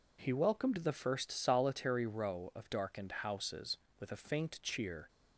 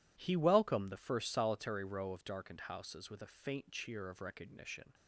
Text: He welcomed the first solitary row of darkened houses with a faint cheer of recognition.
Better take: second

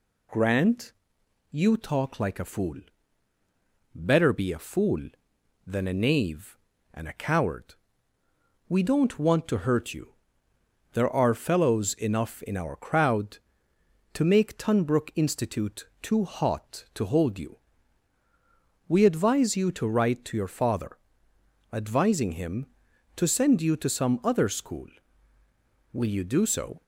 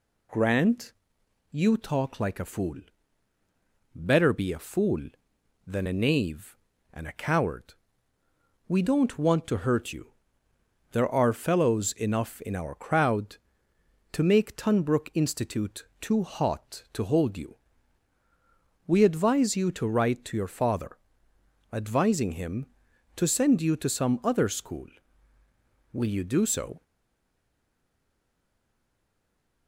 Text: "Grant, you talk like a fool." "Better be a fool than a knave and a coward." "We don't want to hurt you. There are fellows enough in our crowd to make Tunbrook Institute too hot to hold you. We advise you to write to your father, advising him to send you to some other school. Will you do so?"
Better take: first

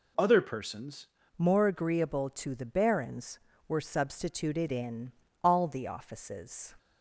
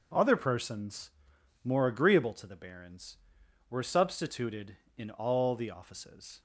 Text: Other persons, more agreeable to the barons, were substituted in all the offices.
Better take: second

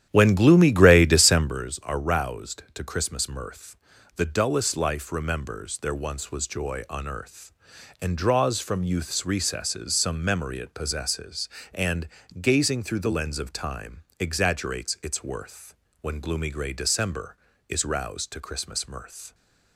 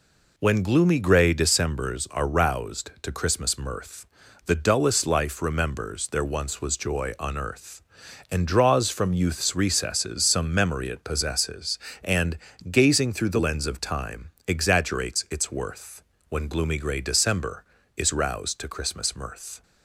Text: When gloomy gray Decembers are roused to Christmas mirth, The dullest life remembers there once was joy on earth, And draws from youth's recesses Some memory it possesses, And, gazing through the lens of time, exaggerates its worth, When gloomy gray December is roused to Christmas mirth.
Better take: second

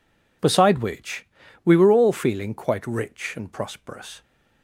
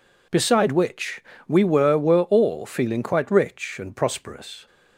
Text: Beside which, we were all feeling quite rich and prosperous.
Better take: first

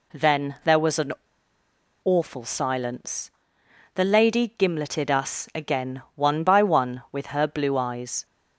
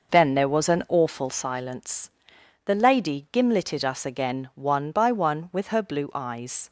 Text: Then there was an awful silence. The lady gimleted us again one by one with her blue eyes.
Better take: second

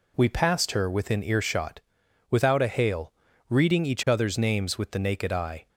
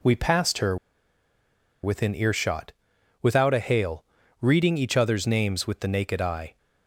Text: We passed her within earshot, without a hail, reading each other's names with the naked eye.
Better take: first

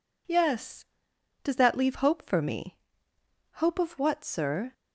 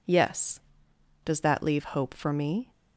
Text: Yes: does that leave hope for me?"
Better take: second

